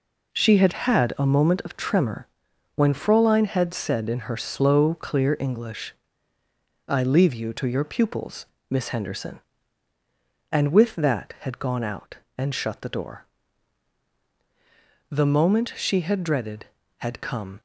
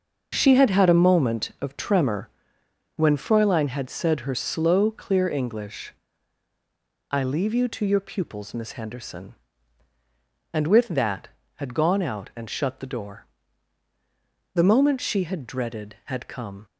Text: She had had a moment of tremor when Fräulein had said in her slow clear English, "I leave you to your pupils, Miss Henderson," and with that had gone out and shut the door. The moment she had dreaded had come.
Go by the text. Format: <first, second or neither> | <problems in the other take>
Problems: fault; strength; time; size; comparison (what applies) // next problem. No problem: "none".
first | starts louder than the rest; until 1.3 s; 6.5 dB // pauses between "tremor" and "when"; noticeable; at 2.2 s; 0.68 s long; noticeable in the first // skips "in"; at 4.2 s